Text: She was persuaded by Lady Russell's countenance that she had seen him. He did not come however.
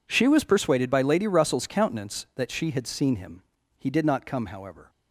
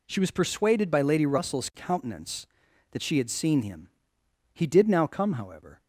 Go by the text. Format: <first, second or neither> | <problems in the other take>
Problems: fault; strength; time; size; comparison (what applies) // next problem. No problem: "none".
first | says "now" for "not"; at 4.8 s